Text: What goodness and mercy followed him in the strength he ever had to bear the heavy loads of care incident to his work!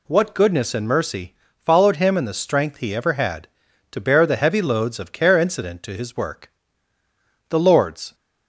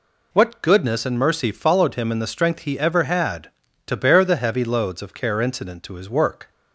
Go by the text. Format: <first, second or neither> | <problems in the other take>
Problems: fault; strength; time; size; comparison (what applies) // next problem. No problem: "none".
second | pauses between "mercy" and "followed"; slight; at 1.3 s; 0.30 s long // goes on to say "The Lord's"; noticeable; from 7.4 s on; 0.66 s long